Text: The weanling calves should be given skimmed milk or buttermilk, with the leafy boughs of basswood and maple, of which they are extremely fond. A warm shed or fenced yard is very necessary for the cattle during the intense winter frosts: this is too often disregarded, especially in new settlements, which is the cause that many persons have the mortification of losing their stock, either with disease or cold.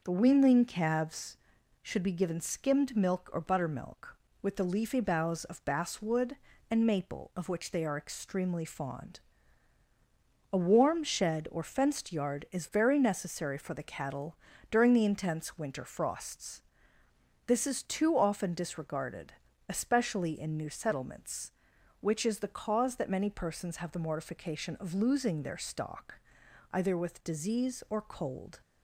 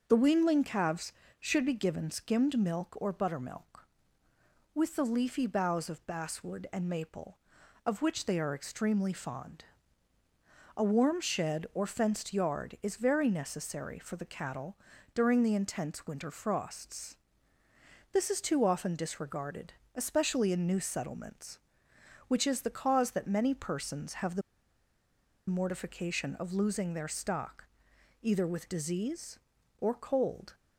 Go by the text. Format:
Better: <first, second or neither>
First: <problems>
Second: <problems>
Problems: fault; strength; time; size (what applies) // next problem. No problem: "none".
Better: first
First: starts louder than the rest; noticeable; until 1.0 s; 6 dB // pauses between "cattle" and "during"; slight; at 14.3 s; 0.32 s long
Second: starts louder than the rest; noticeable; until 1.0 s; 6 dB // pauses between "cattle" and "during"; at 14.7 s; 0.38 s long // pauses between "the" and "mortification"; at 24.4 s; 1.0 s long